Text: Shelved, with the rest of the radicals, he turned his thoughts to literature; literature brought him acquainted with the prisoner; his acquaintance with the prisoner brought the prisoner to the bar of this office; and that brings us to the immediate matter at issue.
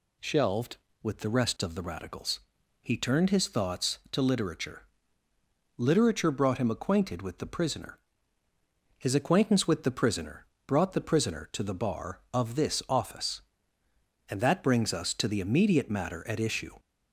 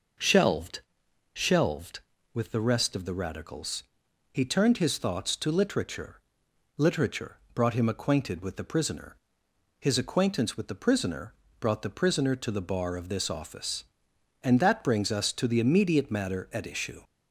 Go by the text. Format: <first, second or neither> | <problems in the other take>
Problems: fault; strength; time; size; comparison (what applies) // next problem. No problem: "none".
first | says "Shelved" twice; at 1.3 s // pauses between "literature" and "brought"; slight; at 7.3 s; 0.18 s long // pauses between "prisoner" and "brought"; slight; at 11.3 s; 0.24 s long; slight in the first